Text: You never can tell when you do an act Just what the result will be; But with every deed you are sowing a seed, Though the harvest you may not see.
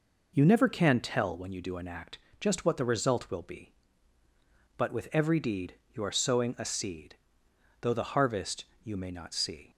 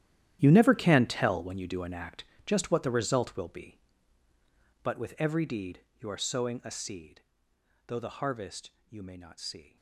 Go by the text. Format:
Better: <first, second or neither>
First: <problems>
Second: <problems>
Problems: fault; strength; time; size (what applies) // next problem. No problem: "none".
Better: first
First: pauses between "act" and "Just"; slight; at 2.1 s; 0.22 s long // pauses between "deed" and "you"; slight; at 5.7 s; 0.18 s long // pauses between "harvest" and "you"; slight; at 8.6 s; 0.18 s long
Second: gets quieter; strong; throughout; 15 dB // pauses between "act" and "Just"; slight; at 2.2 s; 0.22 s long // pauses between "deed" and "you"; slight; at 5.8 s; 0.18 s long // pauses between "harvest" and "you"; slight; at 8.7 s; 0.18 s long